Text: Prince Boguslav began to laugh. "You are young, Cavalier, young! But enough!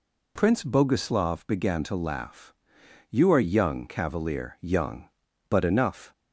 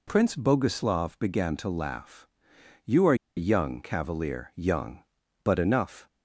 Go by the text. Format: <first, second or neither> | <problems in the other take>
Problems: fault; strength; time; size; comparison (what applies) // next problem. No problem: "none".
first | pauses between "are" and "young"; slight; at 3.1 s; 0.22 s long